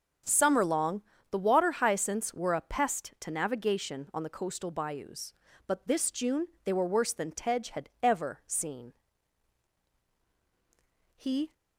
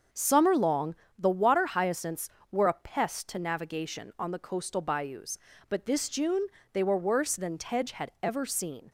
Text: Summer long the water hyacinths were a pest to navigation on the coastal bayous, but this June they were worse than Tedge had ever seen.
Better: second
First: starts louder than the rest; until 1.5 s; 6.5 dB // pauses between "long" and "the"; slight; at 1.0 s; 0.28 s long // pauses between "June" and "they"; slight; at 6.4 s; 0.16 s long // goes on to say "He"; slight; from 11.1 s on; 0.36 s long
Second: starts louder than the rest; until 1.3 s; 6.5 dB // pauses between "long" and "the"; slight; at 0.9 s; 0.24 s long // pauses between "June" and "they"; slight; at 6.4 s; 0.24 s long

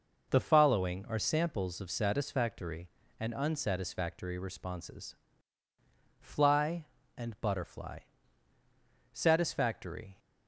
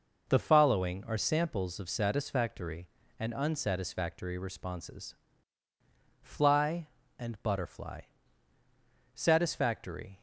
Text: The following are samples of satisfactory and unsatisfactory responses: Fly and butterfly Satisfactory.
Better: neither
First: pauses between "butterfly" and "Satisfactory"; at 8.0 s; 1.1 s long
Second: pauses between "butterfly" and "Satisfactory"; at 8.0 s; 1.1 s long

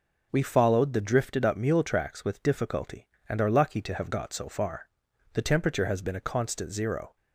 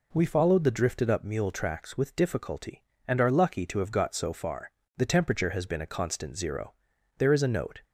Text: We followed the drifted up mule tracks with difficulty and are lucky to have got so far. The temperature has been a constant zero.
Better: first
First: none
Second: goes on to say "There is a note"; noticeable; from 7.1 s on; 0.66 s long

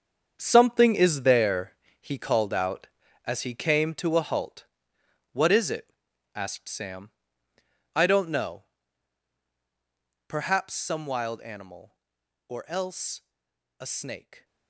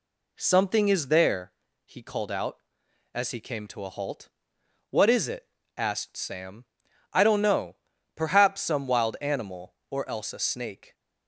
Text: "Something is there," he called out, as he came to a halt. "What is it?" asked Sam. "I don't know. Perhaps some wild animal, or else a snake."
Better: second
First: gets quieter; strong; throughout; 11 dB // pauses between "else" and "a"; noticeable; at 13.2 s; 0.58 s long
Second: none

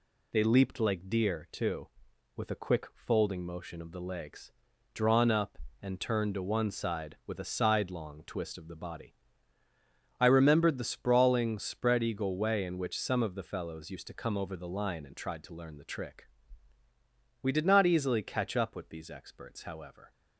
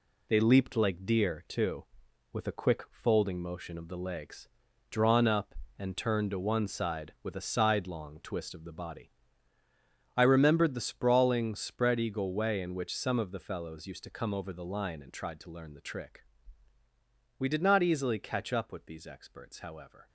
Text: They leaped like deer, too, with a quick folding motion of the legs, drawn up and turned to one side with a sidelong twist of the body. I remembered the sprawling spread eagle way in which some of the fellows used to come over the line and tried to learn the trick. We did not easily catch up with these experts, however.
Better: first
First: none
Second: gets quieter; throughout; 7 dB

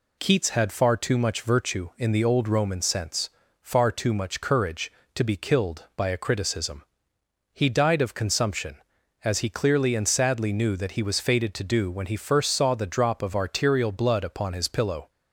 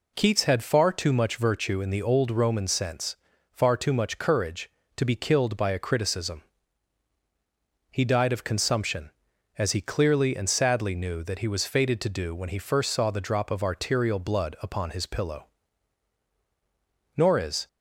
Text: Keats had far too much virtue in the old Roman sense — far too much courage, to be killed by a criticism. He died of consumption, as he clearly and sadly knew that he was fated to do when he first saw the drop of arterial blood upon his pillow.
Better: first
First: none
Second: goes on to say "Nor is"; from 17.1 s on; 0.52 s long

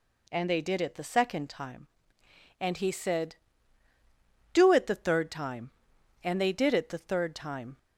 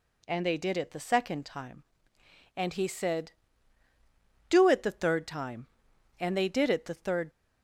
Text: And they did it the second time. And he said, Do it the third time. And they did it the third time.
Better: first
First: none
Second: stops before "time"; at 7.2 s

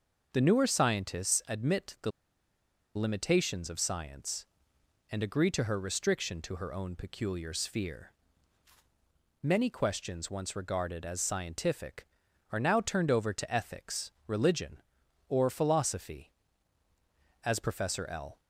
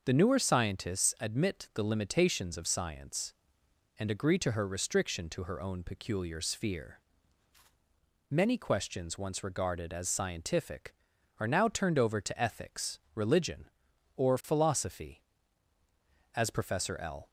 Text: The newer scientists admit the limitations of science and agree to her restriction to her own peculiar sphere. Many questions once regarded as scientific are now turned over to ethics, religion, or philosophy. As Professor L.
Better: second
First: starts louder than the rest; noticeable; until 1.3 s; 6 dB // pauses between "the" and "limitations"; noticeable; at 2.1 s; 0.84 s long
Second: starts louder than the rest; noticeable; until 1.0 s; 6 dB

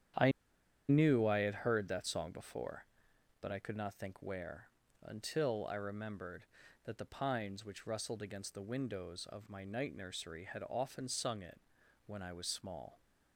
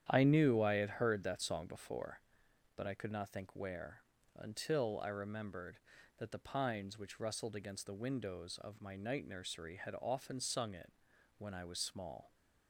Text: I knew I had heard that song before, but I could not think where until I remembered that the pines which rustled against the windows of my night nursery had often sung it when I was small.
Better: second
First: starts louder than the rest; strong; until 1.7 s; 9.5 dB // pauses between "I" and "knew"; noticeable; at 0.3 s; 0.58 s long // pauses between "where" and "until"; slight; at 4.6 s; 0.36 s long // pauses between "it" and "when"; noticeable; at 11.6 s; 0.46 s long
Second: starts louder than the rest; strong; until 1.1 s; 9.5 dB // pauses between "where" and "until"; slight; at 4.0 s; 0.36 s long // pauses between "it" and "when"; noticeable; at 10.9 s; 0.46 s long

